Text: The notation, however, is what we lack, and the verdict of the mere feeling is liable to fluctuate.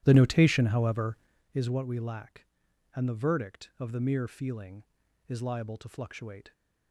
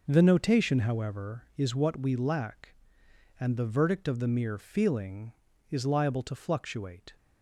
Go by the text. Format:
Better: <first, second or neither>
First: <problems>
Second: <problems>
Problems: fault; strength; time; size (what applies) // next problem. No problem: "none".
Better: second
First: starts louder than the rest; strong; until 1.5 s; 12.5 dB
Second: none